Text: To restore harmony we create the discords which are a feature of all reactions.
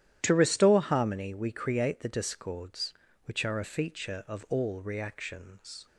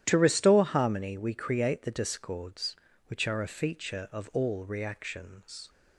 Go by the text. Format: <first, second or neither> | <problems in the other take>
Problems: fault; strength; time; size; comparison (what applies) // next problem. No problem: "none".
neither | starts louder than the rest; strong; the same in both